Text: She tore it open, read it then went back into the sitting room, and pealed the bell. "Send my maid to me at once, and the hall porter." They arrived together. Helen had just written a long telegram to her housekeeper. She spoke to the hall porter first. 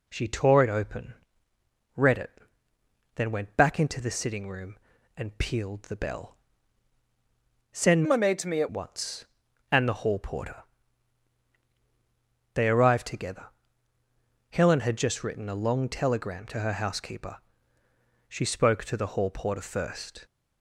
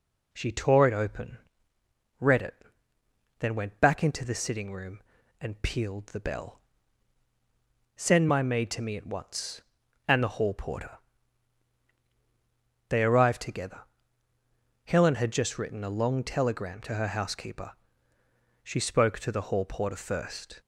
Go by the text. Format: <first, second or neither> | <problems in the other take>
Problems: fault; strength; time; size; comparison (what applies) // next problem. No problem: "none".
second | pauses between "it" and "then"; noticeable; at 2.3 s; 0.84 s long; noticeable in the second // changes voice from "my" to "at"; from 8.0 to 8.6 s; 0.6 s long